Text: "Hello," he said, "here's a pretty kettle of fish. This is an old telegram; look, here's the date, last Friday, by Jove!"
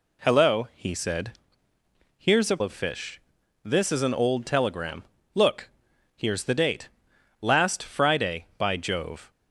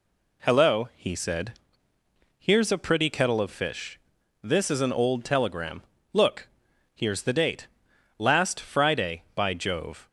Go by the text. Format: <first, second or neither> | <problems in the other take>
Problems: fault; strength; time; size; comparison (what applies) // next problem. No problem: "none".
second | skips "pretty kettle"; at 2.6 s